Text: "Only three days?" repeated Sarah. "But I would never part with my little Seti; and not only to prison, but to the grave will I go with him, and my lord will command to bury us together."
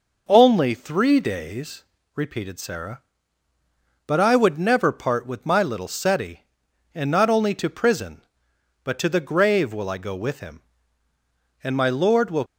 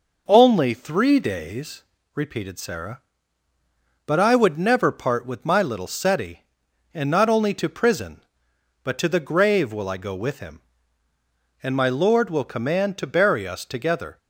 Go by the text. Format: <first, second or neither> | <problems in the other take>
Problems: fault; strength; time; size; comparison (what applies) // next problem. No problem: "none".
second | stops before "command to bury us together"; at 12.4 s